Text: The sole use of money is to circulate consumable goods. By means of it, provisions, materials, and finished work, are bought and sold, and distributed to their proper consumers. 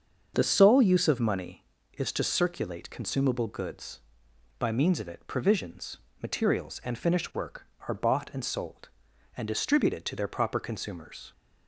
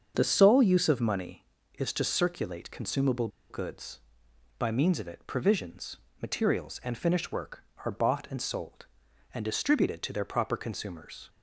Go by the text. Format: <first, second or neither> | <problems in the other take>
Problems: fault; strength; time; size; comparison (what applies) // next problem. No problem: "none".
first | starts louder than the rest; until 1.1 s; 7 dB; also in the first // pauses between "consumable" and "goods"; slight; at 3.2 s; 0.21 s long